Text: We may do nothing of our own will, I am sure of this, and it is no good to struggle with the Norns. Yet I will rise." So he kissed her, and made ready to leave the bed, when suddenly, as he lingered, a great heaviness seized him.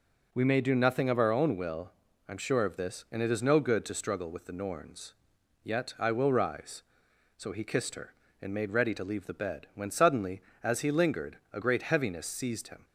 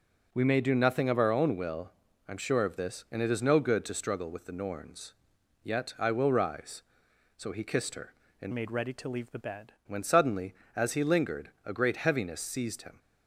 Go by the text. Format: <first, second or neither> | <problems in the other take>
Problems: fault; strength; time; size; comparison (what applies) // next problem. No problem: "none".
first | changes voice from "made" to "bed"; from 8.5 to 9.7 s; 1.2 s long